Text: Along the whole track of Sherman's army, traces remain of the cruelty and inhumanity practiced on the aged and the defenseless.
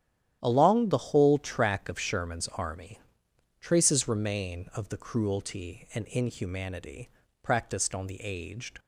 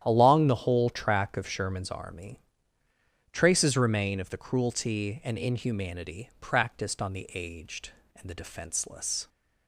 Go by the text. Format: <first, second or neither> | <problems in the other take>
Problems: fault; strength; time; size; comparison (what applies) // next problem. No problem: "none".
second | starts louder than the rest; strong; until 1.4 s; 11 dB; strong in the second // pauses between "inhumanity" and "practiced"; slight; at 7.0 s; 0.36 s long // stops before "and the defenseless"; at 8.7 s